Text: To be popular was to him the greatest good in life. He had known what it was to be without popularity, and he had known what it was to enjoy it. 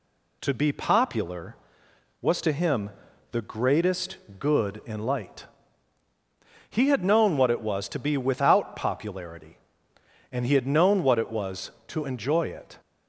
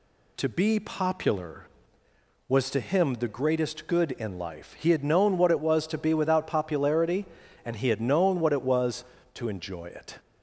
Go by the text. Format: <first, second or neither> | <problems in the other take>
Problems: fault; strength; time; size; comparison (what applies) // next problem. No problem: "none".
second | pauses between "him" and "the"; at 2.8 s; 0.42 s long // pauses between "greatest" and "good"; slight; at 4.1 s; 0.22 s long // says "light" for "life"; at 4.9 s